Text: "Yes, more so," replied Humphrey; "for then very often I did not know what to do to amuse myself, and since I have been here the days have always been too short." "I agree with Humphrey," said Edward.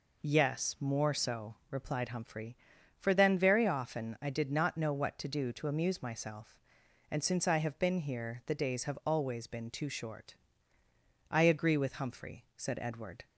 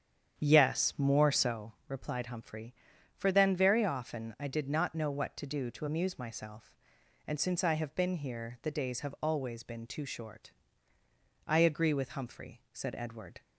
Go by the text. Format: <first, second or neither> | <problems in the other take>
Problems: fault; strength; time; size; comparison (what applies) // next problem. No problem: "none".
first | starts louder than the rest; strong; until 1.7 s; 8.5 dB